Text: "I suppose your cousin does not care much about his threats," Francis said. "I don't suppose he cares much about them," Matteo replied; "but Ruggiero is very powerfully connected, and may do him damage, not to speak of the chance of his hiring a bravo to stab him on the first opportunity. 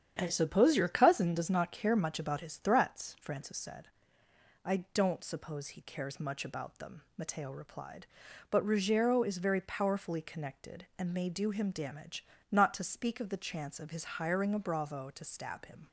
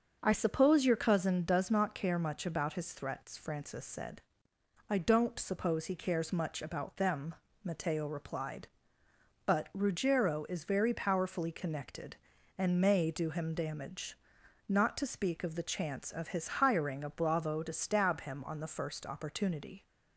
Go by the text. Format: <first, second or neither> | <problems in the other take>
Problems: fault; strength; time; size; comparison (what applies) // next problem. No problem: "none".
second | starts louder than the rest; strong; until 1.2 s; 9 dB; also in the second // pauses between "I" and "don't"; slight; at 4.7 s; 0.16 s long // stops before "on the first opportunity"; at 15.8 s